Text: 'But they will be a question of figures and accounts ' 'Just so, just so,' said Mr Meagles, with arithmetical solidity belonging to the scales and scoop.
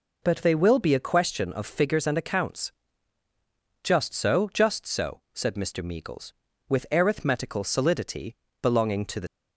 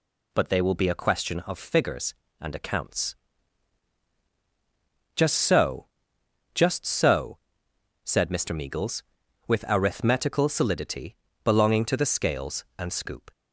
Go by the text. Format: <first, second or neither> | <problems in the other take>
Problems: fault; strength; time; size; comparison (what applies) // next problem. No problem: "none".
second | pauses between "solidity" and "belonging"; slight; at 8.3 s; 0.26 s long; slight in the second // stops before "scales and scoop"; at 9.2 s